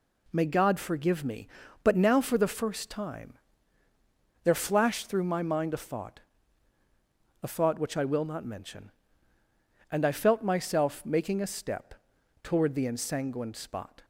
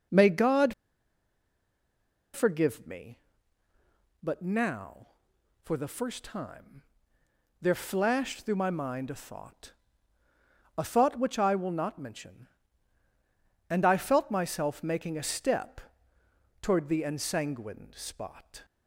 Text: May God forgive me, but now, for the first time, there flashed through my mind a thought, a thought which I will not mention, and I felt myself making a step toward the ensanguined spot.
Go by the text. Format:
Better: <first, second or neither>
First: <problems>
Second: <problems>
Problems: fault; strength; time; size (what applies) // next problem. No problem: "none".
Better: first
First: pauses between "step" and "toward"; noticeable; at 11.9 s; 0.48 s long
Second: pauses between "God" and "forgive"; strong; at 0.7 s; 1.6 s long // pauses between "step" and "toward"; noticeable; at 15.8 s; 0.80 s long